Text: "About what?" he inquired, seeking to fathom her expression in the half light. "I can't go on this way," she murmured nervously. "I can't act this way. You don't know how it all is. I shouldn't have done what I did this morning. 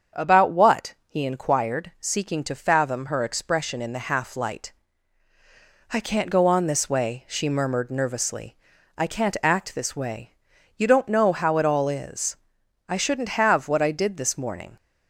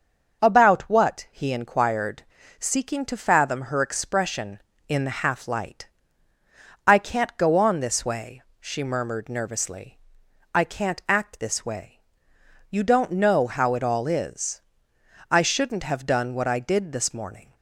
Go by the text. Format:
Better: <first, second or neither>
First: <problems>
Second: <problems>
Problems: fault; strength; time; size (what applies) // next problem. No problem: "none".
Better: second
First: starts louder than the rest; strong; until 1.3 s; 7 dB // skips "done"; at 13.6 s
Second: starts louder than the rest; until 1.4 s; 6.5 dB